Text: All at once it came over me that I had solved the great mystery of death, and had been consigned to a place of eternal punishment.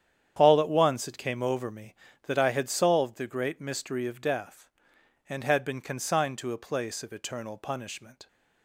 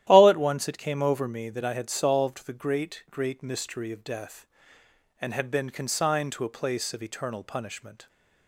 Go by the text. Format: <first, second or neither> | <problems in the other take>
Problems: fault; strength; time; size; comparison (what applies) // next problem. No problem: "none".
first | starts louder than the rest; strong; until 1.0 s; 12.5 dB; strong in the first // says "great" twice; at 3.0 s